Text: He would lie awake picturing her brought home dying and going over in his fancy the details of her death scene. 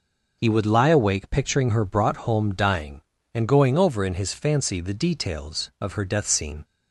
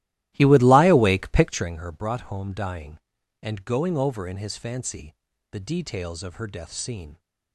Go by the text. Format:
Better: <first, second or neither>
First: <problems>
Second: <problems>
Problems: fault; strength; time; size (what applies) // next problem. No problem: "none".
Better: first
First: none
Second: starts louder than the rest; strong; until 1.8 s; 15.5 dB // pauses between "fancy" and "the"; at 5.1 s; 0.38 s long